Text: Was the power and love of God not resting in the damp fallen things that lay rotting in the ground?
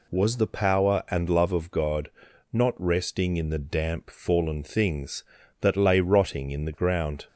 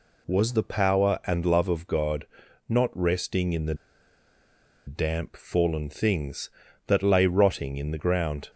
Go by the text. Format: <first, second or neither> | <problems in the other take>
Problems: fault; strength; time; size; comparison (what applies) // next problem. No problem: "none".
first | pauses between "God" and "not"; at 2.2 s; 0.40 s long; also in the first // pauses between "the" and "damp"; at 3.7 s; 1.1 s long